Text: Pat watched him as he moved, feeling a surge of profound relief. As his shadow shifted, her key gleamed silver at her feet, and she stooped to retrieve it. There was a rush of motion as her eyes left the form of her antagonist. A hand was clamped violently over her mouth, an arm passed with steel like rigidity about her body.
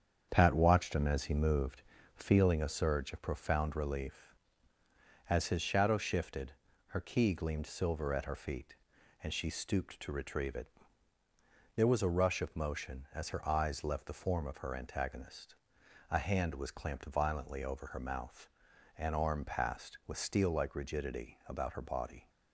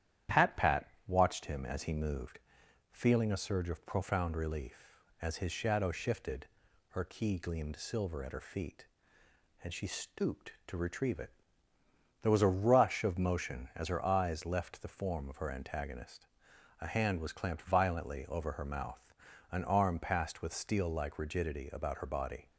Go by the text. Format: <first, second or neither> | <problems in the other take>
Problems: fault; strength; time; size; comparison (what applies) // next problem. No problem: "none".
first | starts louder than the rest; strong; until 1.5 s; 11 dB; strong in the first // says "Pat" twice; at 0.5 s